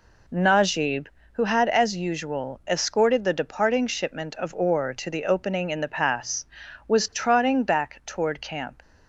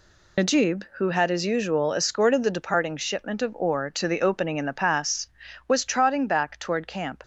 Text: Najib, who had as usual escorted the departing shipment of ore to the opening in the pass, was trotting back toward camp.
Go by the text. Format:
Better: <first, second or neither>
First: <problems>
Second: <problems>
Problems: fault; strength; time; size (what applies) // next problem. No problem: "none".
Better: first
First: none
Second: loses the start of "Najib"; at 0.3 s; 70 ms